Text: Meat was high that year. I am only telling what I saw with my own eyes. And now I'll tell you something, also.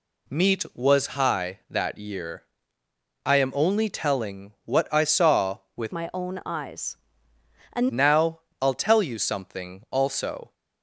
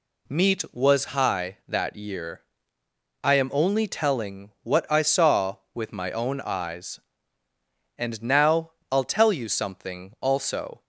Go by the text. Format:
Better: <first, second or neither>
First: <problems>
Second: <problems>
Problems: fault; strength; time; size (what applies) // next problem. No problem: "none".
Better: second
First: changes voice from "my" to "And"; from 5.9 to 7.8 s; 1.9 s long // pauses between "now" and "I'll"; slight; at 8.3 s; 0.20 s long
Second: pauses between "now" and "I'll"; slight; at 8.7 s; 0.18 s long